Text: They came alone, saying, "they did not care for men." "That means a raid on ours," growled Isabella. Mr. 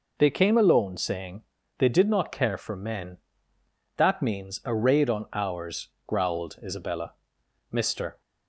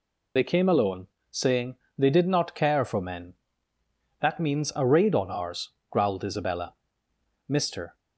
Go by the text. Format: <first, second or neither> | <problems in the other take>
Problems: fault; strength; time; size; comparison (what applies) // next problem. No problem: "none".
first | loses the start of "They"; at 0.3 s; 40 ms